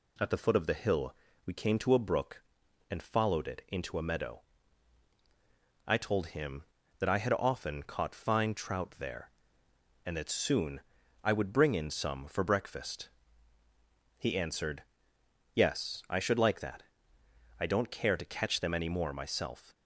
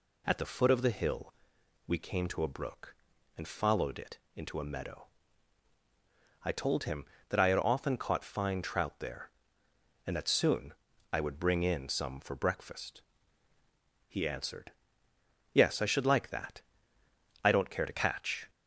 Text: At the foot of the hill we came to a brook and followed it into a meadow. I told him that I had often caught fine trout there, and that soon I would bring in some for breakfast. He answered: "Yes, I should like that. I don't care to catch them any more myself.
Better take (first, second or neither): first